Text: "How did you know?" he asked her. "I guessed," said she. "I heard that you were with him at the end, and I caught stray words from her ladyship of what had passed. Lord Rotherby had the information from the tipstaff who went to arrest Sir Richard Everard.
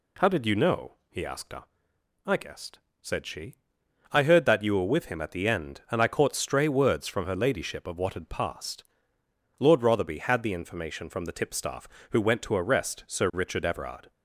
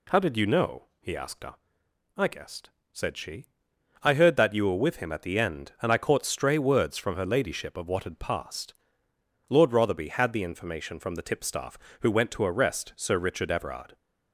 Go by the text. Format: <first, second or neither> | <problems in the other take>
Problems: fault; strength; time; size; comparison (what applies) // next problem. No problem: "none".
neither | none